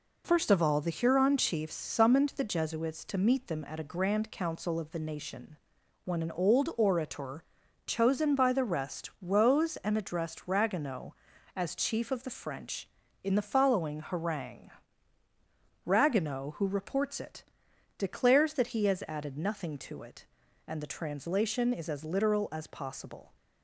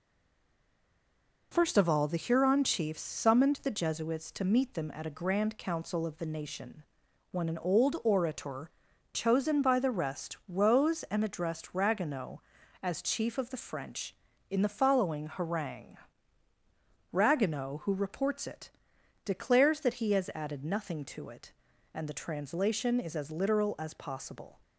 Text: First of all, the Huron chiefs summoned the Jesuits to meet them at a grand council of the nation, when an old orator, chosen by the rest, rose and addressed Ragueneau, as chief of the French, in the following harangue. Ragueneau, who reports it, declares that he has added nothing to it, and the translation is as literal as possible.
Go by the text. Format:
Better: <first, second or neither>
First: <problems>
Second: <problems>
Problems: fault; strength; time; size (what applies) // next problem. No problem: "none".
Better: first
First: none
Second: stays silent before the first word; noticeable; until 1.5 s; 1.5 s long